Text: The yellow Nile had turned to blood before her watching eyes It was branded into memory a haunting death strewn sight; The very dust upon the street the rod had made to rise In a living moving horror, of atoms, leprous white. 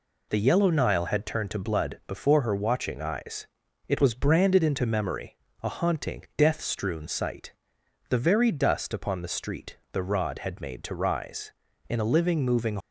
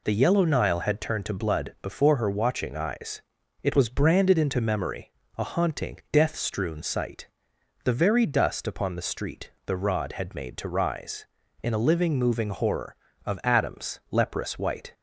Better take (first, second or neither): second